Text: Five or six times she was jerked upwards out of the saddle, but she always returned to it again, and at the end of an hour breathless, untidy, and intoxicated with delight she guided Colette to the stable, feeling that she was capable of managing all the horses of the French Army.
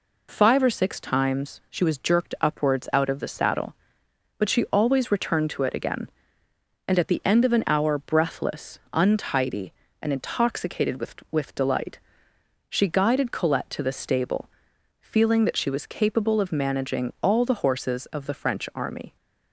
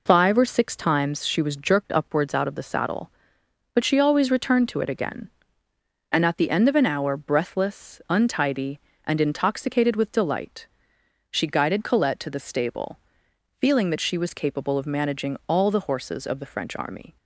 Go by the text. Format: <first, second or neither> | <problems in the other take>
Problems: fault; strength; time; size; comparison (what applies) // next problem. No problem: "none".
second | says "with" twice; at 11.3 s // pauses between "delight" and "she"; noticeable; at 11.9 s; 0.70 s long; noticeable in the second